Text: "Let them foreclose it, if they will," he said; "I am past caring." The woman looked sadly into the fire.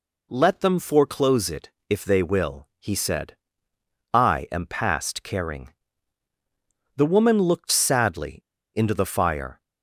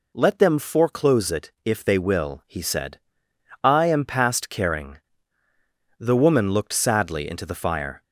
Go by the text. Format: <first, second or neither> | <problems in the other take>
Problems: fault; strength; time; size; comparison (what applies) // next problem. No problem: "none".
second | pauses between "sadly" and "into"; at 8.3 s; 0.37 s long